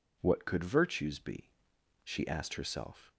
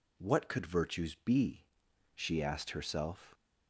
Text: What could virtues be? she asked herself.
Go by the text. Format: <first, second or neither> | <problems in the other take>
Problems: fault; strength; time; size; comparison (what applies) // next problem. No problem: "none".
neither | none